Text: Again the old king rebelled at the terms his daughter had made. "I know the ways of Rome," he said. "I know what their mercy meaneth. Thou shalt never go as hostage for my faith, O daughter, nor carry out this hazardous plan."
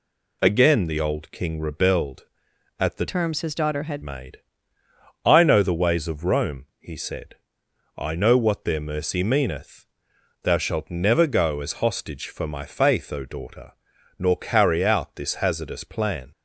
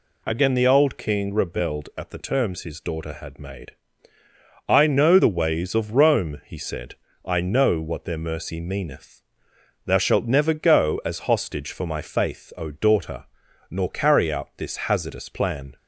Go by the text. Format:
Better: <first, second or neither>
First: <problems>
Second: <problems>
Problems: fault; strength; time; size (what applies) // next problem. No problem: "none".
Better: second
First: changes voice from "terms" to "had"; from 3.0 to 4.0 s; 1.0 s long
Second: none